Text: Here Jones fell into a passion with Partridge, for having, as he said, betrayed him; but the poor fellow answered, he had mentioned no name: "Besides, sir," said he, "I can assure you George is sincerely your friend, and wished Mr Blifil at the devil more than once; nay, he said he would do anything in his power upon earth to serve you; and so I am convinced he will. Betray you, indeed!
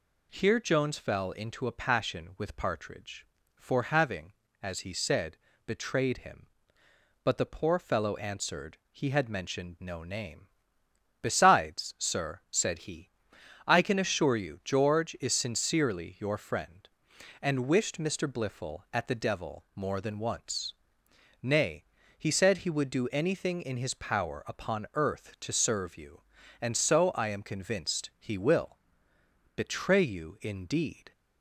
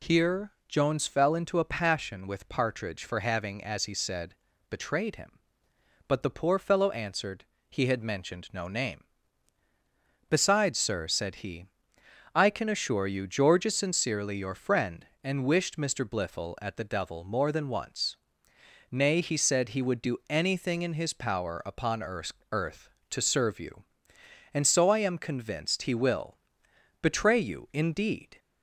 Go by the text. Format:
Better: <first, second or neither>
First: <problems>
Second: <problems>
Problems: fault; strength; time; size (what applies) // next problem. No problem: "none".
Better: first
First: none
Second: pauses between "Here" and "Jones"; slight; at 0.5 s; 0.16 s long // says "earth" twice; at 22.5 s